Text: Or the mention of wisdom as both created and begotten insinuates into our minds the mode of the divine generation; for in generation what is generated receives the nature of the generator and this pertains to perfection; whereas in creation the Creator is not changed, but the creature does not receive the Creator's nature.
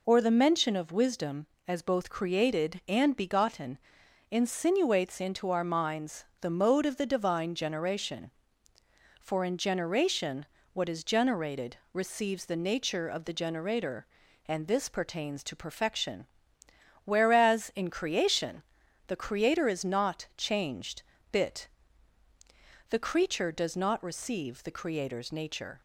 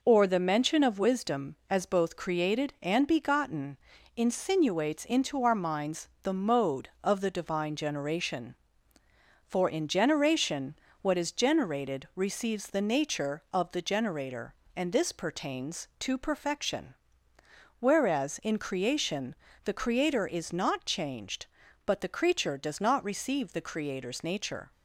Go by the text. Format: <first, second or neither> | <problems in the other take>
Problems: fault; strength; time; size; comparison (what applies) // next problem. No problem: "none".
second | pauses between "begotten" and "insinuates"; noticeable; at 3.7 s; 0.52 s long; also in the second // pauses between "minds" and "the"; slight; at 6.2 s; 0.16 s long // pauses between "generation" and "what"; slight; at 10.4 s; 0.30 s long; slight in the second // pauses between "generated" and "receives"; slight; at 11.7 s; 0.18 s long // pauses between "creation" and "the"; at 18.6 s; 0.44 s long; slight in the second // says "bit" for "but"; at 21.3 s